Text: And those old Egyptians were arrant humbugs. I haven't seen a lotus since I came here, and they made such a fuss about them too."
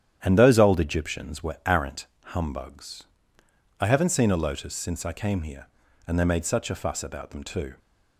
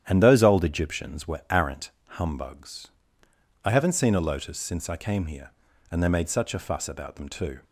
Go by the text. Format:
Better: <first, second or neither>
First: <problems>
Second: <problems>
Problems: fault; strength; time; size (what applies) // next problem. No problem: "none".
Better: neither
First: starts louder than the rest; strong; until 1.2 s; 10 dB // pauses between "arrant" and "humbugs"; slight; at 2.0 s; 0.20 s long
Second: starts louder than the rest; strong; until 1.0 s; 10 dB // pauses between "arrant" and "humbugs"; slight; at 1.8 s; 0.20 s long